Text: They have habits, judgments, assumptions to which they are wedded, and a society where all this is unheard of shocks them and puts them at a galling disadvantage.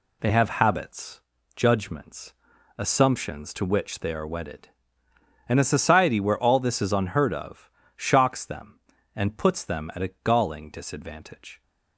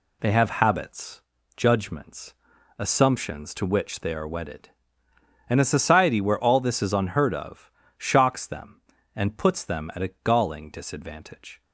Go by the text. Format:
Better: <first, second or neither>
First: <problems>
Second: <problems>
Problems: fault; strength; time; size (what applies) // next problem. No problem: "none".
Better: neither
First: pauses between "of" and "shocks"; slight; at 7.7 s; 0.24 s long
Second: pauses between "of" and "shocks"; slight; at 7.7 s; 0.25 s long